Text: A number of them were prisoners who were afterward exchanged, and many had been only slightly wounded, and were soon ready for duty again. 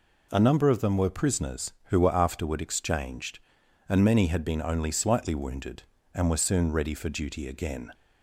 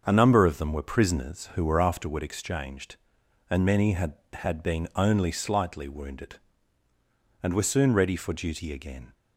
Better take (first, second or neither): first